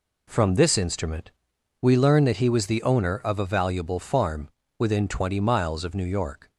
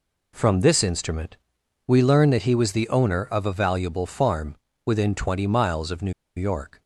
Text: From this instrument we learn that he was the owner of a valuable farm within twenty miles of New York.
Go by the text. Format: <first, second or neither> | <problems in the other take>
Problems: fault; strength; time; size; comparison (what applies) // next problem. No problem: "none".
first | pauses between "instrument" and "we"; noticeable; at 1.3 s; 0.50 s long; noticeable in the first // pauses between "farm" and "within"; slight; at 4.5 s; 0.28 s long; slight in the first // pauses between "New" and "York"; slight; at 6.1 s; 0.24 s long